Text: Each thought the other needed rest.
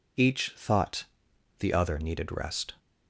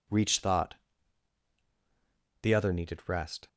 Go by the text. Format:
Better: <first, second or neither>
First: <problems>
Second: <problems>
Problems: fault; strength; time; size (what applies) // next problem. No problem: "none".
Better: first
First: pauses between "thought" and "the"; noticeable; at 1.0 s; 0.54 s long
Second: says "Reach" for "Each"; at 0.0 s // pauses between "thought" and "the"; strong; at 0.7 s; 1.6 s long